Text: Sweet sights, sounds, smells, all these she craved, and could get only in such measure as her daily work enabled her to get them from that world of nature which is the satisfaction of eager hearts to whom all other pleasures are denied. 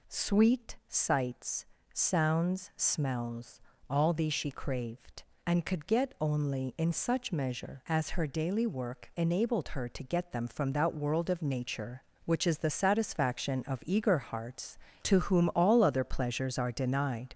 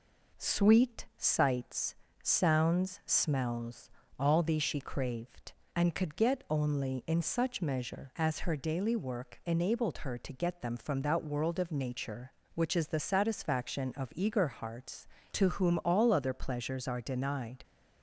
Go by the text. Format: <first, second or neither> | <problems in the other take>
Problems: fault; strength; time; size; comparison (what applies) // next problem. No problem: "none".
second | gets louder; noticeable; throughout; 4.5 dB